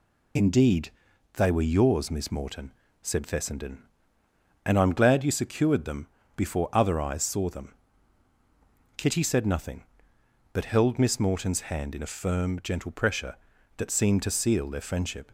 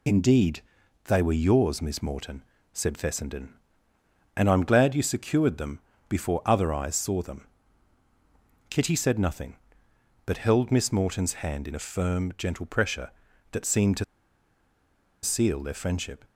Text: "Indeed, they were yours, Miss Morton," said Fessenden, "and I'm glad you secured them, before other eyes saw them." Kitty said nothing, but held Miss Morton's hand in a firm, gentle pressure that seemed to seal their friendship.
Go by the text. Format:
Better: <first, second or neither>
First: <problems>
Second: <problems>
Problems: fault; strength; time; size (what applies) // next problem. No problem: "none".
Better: first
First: none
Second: pauses between "to" and "seal"; at 14.0 s; 1.1 s long